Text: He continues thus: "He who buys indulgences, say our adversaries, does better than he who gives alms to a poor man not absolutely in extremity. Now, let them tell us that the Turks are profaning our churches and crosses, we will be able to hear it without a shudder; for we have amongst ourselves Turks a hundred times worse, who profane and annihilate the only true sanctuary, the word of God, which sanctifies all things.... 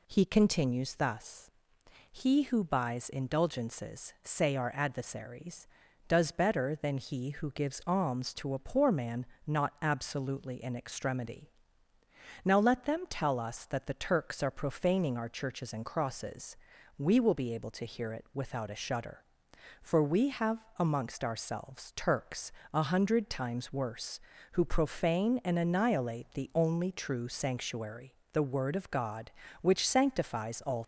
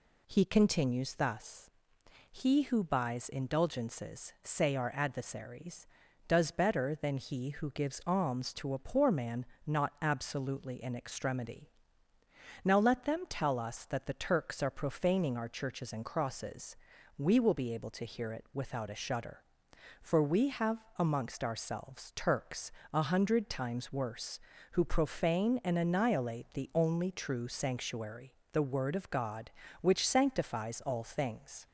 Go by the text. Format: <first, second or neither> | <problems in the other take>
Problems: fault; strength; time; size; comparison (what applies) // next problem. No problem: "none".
second | pauses between "man" and "not"; slight; at 9.2 s; 0.22 s long; slight in the second // pauses between "Turks" and "a"; slight; at 22.5 s; 0.22 s long; slight in the second // stops before "things"; at 30.8 s